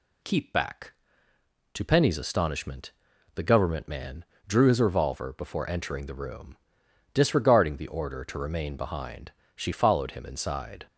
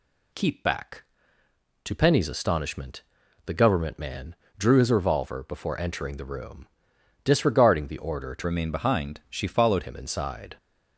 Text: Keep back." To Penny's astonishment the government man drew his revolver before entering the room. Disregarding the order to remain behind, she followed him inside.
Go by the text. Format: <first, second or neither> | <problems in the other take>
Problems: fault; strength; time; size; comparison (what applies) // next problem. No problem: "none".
first | pauses between "astonishment" and "the"; at 3.0 s; 0.42 s long; also in the first // pauses between "man" and "drew"; slight; at 4.3 s; 0.22 s long; slight in the first // changes voice from "remain" to "followed"; from 8.4 to 9.8 s; 1.4 s long